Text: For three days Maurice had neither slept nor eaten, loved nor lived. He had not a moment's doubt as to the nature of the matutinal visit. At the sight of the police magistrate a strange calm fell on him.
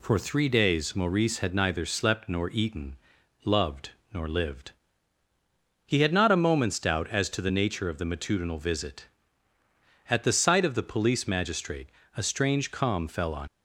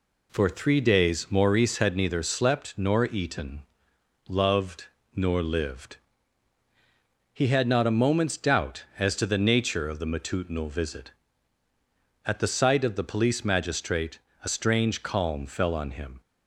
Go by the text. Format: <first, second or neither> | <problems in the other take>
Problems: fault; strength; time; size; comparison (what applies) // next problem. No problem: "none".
second | pauses between "loved" and "nor"; slight; at 3.9 s; 0.20 s long; slight in the second // pauses between "magistrate" and "a"; slight; at 11.8 s; 0.26 s long; slight in the second // stops before "him"; at 13.4 s